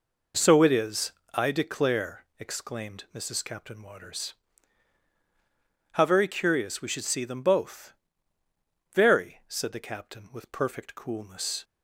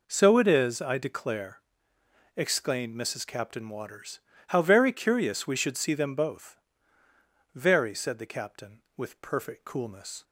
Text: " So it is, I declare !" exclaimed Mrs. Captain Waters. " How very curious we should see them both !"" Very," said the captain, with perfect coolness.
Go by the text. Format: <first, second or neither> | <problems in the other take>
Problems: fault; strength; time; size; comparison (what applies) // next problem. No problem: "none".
neither | none